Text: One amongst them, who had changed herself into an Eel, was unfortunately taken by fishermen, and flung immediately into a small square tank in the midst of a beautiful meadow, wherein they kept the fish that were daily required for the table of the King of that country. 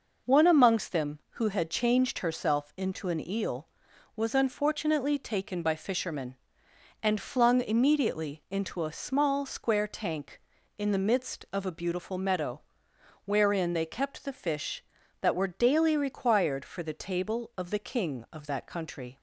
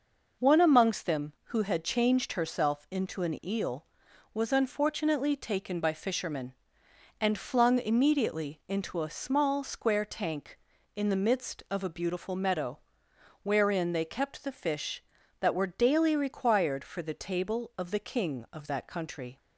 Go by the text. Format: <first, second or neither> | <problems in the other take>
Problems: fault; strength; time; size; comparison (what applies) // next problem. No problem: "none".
neither | none